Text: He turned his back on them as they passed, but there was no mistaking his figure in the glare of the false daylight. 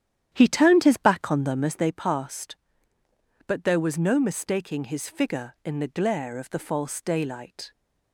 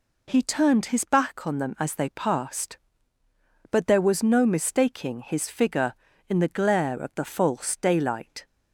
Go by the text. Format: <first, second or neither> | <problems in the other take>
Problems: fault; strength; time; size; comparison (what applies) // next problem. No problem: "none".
second | starts louder than the rest; strong; until 1.8 s; 10.5 dB